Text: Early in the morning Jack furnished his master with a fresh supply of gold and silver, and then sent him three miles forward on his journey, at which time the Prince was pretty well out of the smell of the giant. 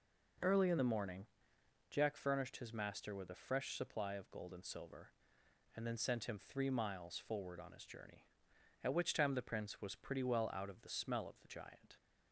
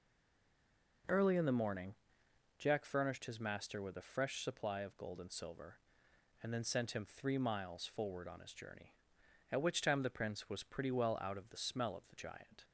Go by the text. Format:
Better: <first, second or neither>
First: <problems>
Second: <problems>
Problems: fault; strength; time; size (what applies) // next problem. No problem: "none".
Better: first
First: pauses between "morning" and "Jack"; noticeable; at 1.2 s; 0.64 s long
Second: stays silent before the first word; until 1.0 s; 1.0 s long // pauses between "morning" and "Jack"; noticeable; at 1.9 s; 0.64 s long